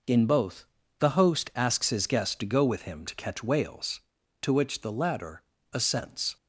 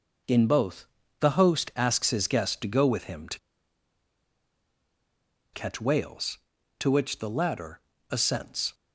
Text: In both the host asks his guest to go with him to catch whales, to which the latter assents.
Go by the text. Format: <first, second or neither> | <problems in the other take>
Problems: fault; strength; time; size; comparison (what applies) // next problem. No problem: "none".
first | pauses between "both" and "the"; slight; at 0.8 s; 0.34 s long; slight in the first // pauses between "to" and "catch"; strong; at 3.3 s; 2.1 s long // pauses between "latter" and "assents"; slight; at 7.7 s; 0.32 s long; slight in the first